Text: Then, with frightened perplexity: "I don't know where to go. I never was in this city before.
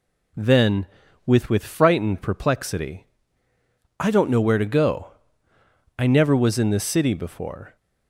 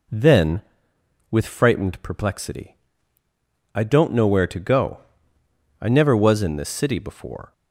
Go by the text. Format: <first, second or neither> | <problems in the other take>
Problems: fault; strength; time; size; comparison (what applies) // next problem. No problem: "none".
second | says "with" twice; at 1.4 s